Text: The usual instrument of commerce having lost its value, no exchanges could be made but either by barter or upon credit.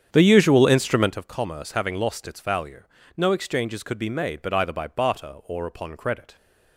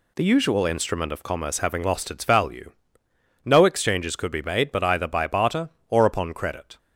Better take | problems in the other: second | starts louder than the rest; strong; until 1.2 s; 8.5 dB

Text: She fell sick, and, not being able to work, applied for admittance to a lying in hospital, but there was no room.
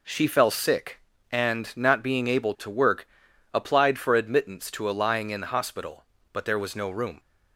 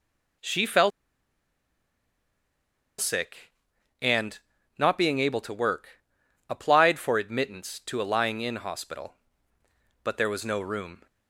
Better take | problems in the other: first | pauses between "fell" and "sick"; strong; at 0.9 s; 2.0 s long

